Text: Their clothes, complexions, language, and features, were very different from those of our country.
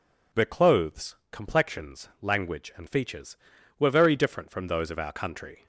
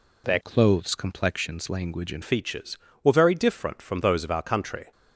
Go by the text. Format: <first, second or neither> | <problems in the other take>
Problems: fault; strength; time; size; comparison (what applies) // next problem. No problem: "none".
first | changes voice from "clothes" to "and"; from 0.4 to 2.2 s; 1.8 s long